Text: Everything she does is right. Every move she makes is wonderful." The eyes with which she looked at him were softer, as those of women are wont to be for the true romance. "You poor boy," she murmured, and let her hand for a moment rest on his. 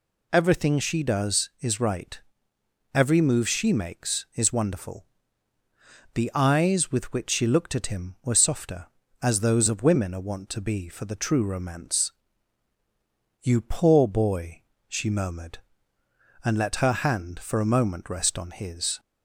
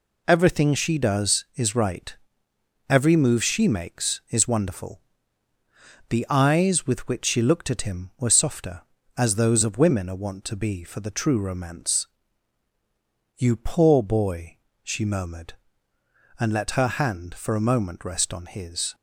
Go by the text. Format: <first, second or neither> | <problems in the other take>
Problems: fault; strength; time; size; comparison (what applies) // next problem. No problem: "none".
first | gets quieter; throughout; 6.5 dB